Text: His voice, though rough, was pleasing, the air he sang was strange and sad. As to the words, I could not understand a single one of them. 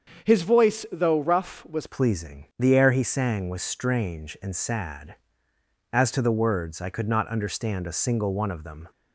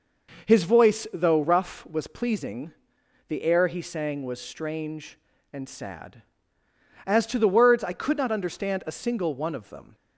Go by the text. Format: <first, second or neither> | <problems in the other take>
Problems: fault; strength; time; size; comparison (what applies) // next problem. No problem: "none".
second | starts louder than the rest; until 1.3 s; 7 dB; noticeable in the second // changes voice at "pleasing"; from 1.8 s on; 7.0 s long